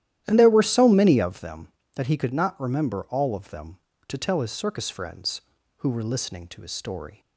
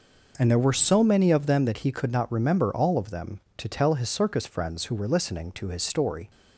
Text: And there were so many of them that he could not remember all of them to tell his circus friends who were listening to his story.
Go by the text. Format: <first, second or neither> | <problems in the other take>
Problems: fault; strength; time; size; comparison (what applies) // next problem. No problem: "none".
second | starts louder than the rest; strong; until 1.4 s; 12.5 dB